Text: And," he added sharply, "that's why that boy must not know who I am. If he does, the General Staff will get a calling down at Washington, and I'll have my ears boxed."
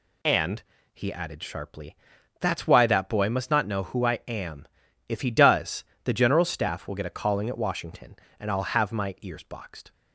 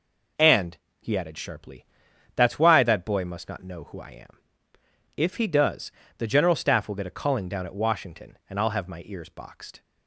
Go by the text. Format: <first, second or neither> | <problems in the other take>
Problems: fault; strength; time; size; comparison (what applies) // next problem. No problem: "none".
second | skips "down"; at 7.4 s